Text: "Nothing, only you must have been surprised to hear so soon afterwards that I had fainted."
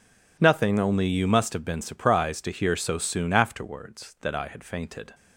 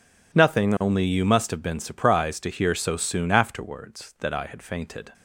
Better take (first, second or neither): neither